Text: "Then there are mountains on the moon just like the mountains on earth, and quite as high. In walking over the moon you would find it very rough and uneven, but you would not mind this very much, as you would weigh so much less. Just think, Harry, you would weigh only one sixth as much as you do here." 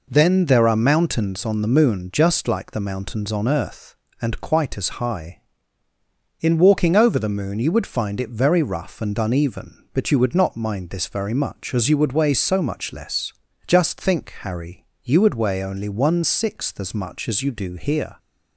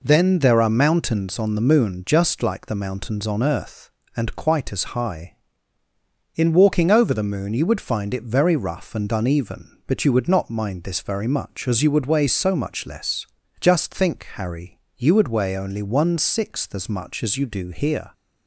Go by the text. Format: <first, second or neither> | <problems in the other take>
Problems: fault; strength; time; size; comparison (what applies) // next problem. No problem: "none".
neither | none